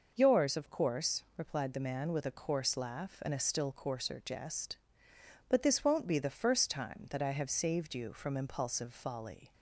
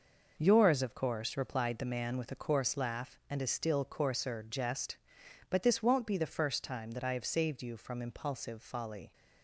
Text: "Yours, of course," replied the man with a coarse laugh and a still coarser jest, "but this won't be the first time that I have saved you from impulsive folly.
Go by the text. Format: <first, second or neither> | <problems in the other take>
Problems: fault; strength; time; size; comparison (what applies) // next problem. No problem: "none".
neither | none